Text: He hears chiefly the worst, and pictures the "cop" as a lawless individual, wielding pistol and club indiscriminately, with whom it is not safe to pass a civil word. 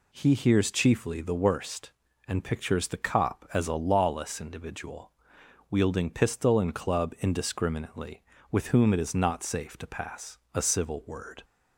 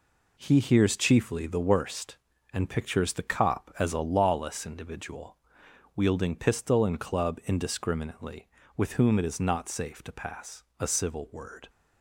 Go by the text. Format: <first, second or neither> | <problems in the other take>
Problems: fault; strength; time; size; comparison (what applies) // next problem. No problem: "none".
first | gets quieter; throughout; 7 dB // pauses between "pass" and "a"; slight; at 10.6 s; 0.16 s long; slight in the first